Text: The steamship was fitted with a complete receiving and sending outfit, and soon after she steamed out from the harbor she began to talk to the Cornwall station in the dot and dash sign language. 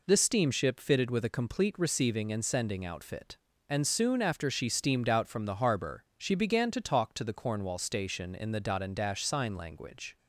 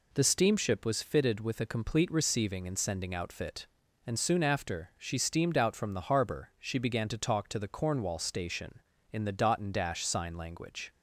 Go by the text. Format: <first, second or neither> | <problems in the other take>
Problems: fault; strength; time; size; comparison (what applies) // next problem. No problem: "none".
second | skips "was"; at 0.8 s